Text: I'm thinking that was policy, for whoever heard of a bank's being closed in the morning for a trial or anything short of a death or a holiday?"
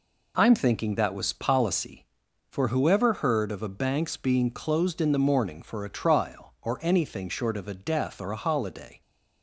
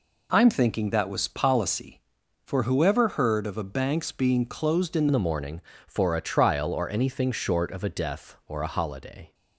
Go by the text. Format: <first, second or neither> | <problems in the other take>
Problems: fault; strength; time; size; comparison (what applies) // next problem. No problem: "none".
first | changes voice at "the"; from 5.1 s on; 4.2 s long